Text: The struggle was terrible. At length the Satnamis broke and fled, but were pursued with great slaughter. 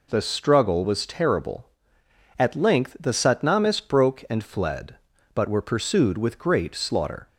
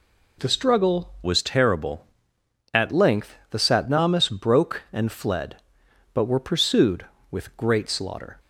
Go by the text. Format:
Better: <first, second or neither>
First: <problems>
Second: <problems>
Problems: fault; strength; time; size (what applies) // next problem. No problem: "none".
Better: first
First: none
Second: changes voice from "was" to "At"; from 1.2 to 2.9 s; 1.7 s long // pauses between "length" and "the"; slight; at 3.3 s; 0.16 s long